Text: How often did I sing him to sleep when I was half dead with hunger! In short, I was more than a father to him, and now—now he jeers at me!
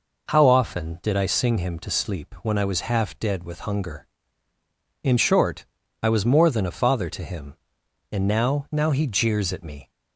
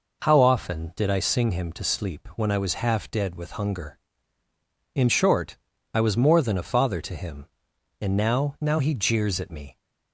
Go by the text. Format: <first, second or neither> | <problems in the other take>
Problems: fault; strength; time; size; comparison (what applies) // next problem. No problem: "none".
neither | none